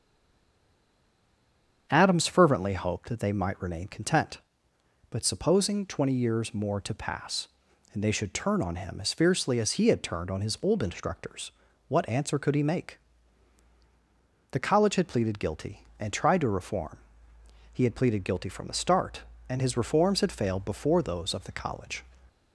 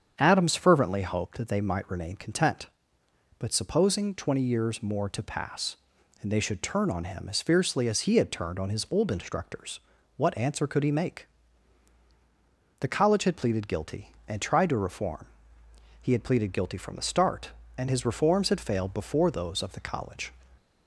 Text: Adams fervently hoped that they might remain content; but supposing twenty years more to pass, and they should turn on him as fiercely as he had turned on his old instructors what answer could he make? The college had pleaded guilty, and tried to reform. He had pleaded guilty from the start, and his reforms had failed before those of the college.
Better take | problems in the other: second | stays silent before the first word; noticeable; until 1.8 s; 1.8 s long // starts louder than the rest; strong; until 2.9 s; 7.5 dB; strong in the second // pauses between "instructors" and "what"; slight; at 11.5 s; 0.36 s long; slight in the second

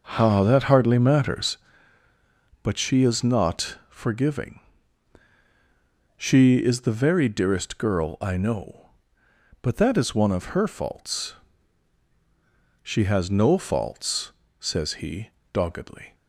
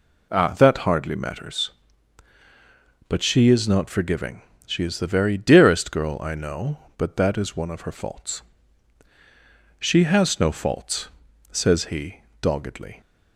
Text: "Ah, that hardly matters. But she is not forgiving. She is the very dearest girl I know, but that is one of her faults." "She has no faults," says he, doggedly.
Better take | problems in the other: second | starts louder than the rest; noticeable; until 1.6 s; 5.5 dB

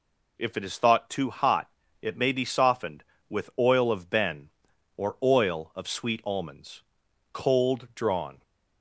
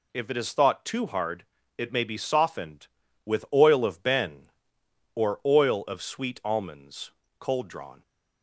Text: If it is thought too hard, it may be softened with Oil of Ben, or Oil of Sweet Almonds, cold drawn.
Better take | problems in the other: second | says "hot" for "hard"; at 1.2 s

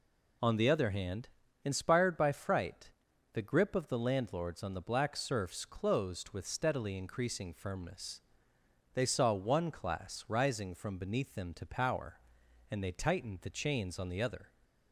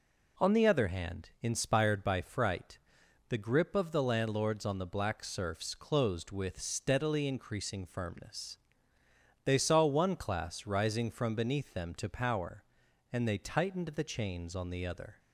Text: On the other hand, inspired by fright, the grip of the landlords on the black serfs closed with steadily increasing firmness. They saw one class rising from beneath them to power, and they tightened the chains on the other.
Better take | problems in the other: neither | none

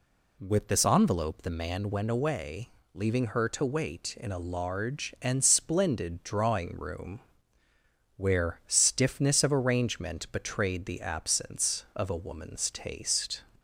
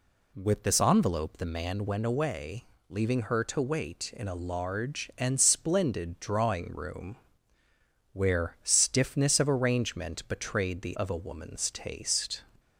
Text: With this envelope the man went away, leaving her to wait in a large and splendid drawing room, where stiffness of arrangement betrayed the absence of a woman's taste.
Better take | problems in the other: first | skips "absence"; at 10.9 s

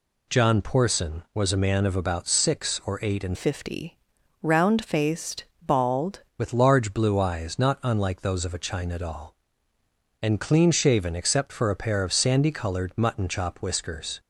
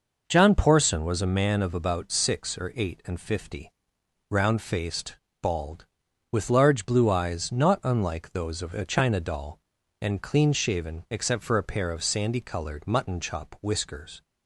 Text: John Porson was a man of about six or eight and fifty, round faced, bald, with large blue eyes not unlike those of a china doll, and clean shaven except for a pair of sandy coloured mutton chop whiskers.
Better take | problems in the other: second | changes voice from "fifty" to "bald"; from 3.3 to 6.2 s; 2.9 s long

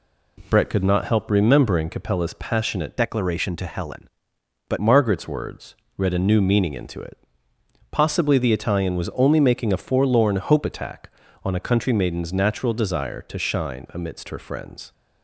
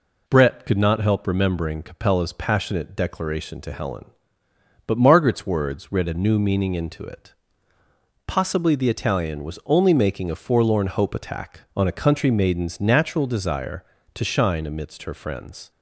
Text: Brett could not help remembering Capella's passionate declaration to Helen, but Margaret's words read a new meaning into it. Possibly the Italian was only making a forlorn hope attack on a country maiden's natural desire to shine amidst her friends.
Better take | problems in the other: second | changes voice from "declaration" to "but"; from 2.9 to 4.7 s; 1.8 s long // pauses between "words" and "read"; slight; at 5.7 s; 0.22 s long

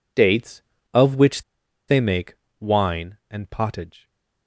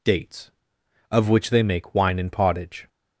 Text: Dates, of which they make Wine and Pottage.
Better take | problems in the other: second | pauses between "which" and "they"; noticeable; at 1.4 s; 0.45 s long // pauses between "make" and "Wine"; slight; at 2.3 s; 0.24 s long

